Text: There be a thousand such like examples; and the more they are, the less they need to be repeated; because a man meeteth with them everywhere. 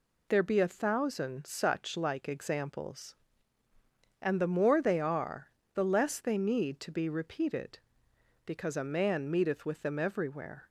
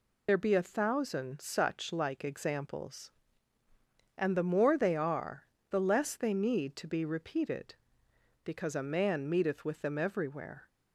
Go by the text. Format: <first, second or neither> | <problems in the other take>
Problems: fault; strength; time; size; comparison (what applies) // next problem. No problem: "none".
first | loses the start of "There"; at 0.2 s; 40 ms